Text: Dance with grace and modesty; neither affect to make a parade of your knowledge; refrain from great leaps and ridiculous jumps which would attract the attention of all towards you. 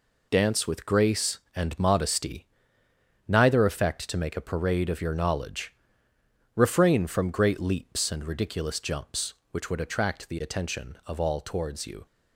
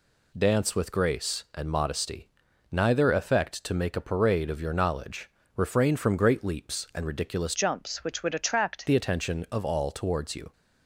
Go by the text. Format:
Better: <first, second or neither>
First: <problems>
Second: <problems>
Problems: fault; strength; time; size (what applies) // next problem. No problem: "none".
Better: first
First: none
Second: changes voice from "jumps" to "attract"; from 7.5 to 8.8 s; 1.3 s long